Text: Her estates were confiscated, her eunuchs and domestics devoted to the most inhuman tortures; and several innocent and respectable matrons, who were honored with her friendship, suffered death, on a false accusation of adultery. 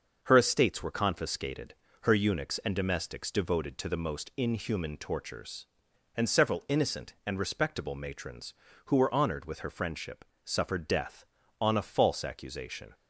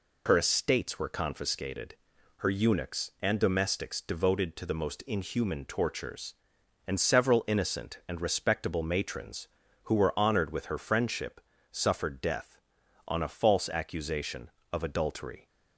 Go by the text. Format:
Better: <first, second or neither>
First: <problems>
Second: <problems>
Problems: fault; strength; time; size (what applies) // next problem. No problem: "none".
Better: second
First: starts louder than the rest; until 1.2 s; 6 dB // stops before "of adultery"; at 12.9 s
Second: none